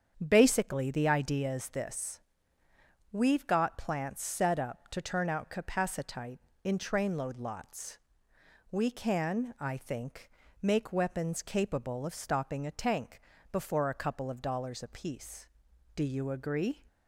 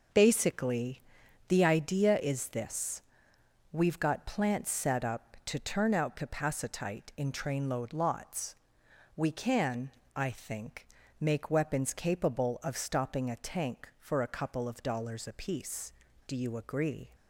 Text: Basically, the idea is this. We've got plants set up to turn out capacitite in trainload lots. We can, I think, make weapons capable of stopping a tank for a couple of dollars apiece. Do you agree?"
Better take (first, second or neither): second